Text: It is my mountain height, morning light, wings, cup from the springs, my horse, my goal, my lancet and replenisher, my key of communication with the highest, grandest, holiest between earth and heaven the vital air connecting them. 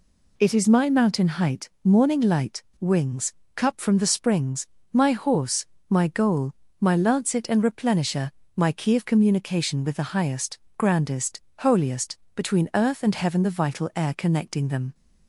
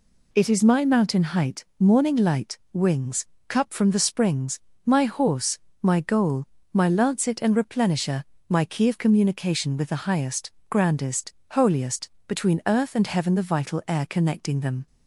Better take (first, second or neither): neither